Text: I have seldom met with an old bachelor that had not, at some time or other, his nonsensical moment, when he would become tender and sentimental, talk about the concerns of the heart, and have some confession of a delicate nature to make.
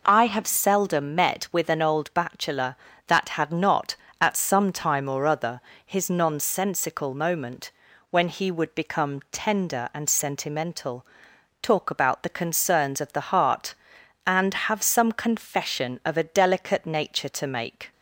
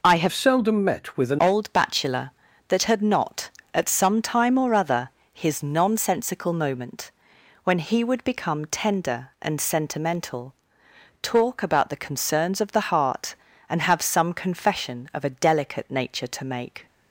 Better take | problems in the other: first | changes voice from "seldom" to "an"; from 0.3 to 1.3 s; 1.0 s long

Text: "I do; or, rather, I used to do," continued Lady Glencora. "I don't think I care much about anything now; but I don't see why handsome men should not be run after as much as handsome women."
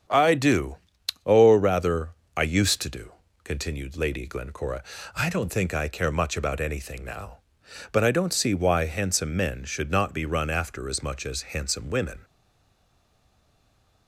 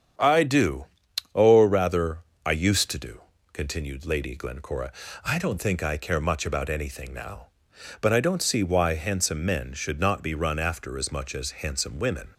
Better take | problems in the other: second | starts louder than the rest; strong; until 1.6 s; 8 dB; strong in the second // stays silent after the last word; noticeable; from 12.2 s on; 1.8 s long

